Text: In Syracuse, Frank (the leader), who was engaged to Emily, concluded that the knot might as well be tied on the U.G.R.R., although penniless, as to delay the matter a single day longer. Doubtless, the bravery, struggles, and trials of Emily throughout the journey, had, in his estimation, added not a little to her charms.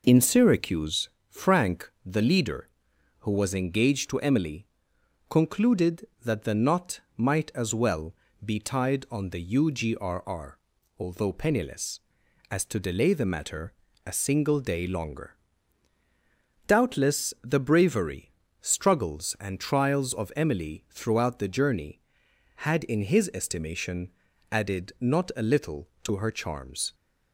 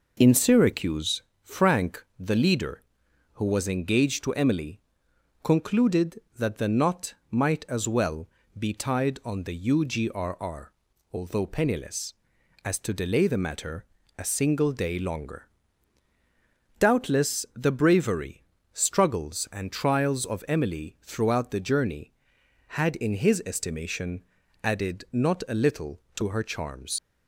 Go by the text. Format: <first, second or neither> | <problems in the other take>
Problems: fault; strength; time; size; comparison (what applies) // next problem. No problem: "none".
first | pauses between "knot" and "might"; slight; at 7.1 s; 0.16 s long; slight in the first // pauses between "well" and "be"; slight; at 8.2 s; 0.32 s long; slight in the first // pauses between "matter" and "a"; slight; at 13.8 s; 0.32 s long; slight in the first // leaves "charms" unfinished; at 26.9 s; 80 ms